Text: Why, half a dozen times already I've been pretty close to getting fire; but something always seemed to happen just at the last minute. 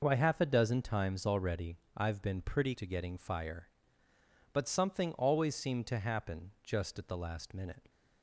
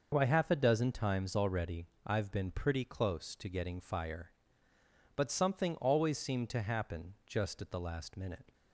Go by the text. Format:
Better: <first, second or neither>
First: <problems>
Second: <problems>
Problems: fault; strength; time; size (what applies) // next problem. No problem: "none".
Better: second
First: pauses between "already" and "I've"; slight; at 1.7 s; 0.18 s long // skips "close"; at 2.7 s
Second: pauses between "already" and "I've"; slight; at 1.8 s; 0.18 s long